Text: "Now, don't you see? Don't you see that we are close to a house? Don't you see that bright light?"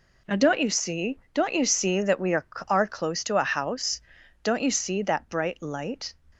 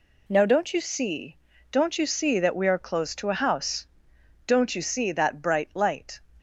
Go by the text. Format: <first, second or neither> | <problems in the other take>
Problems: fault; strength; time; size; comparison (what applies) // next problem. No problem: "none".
second | says "are" twice; at 2.6 s